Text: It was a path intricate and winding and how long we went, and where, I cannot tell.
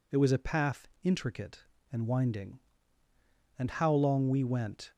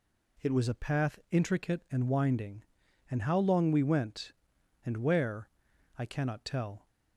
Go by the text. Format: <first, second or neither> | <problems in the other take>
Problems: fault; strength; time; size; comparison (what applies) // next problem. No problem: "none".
second | pauses between "path" and "intricate"; slight; at 0.8 s; 0.16 s long // stops before "and where I cannot tell"; at 4.9 s